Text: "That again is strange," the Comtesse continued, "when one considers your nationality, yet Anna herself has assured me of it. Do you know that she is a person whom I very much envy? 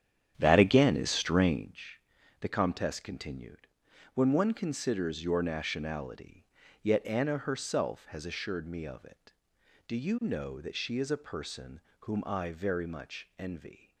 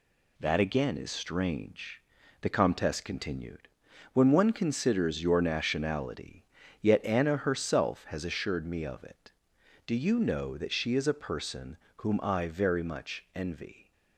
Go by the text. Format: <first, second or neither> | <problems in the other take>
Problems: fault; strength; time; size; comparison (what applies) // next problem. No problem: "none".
second | starts louder than the rest; strong; until 1.8 s; 9.5 dB // pauses between "person" and "whom"; slight; at 11.8 s; 0.20 s long; slight in the second